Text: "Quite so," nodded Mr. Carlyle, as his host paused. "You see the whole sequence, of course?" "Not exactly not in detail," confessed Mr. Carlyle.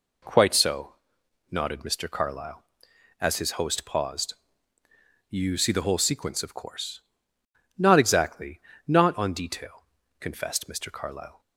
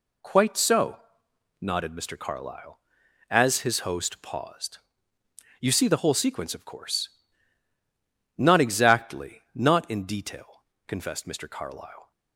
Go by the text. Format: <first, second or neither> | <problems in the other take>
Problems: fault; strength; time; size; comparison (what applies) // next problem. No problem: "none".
second | pauses between "exactly" and "not"; slight; at 8.6 s; 0.26 s long // says "on" for "in"; at 9.1 s